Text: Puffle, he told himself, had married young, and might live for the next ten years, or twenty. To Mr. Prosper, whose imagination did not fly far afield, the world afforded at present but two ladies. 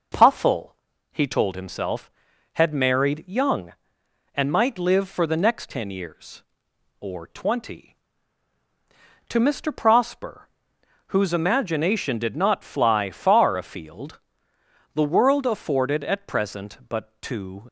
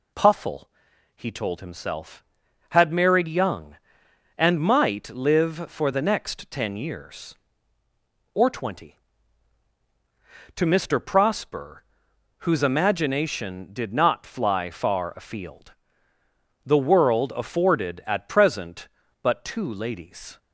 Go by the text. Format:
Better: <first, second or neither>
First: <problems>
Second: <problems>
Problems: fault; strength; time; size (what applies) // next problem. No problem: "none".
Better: second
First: stops before "ladies"; at 17.6 s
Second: none